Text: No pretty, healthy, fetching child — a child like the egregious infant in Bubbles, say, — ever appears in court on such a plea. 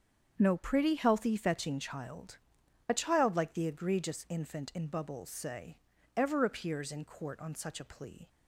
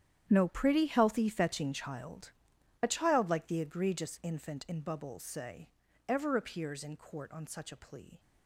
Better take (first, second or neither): first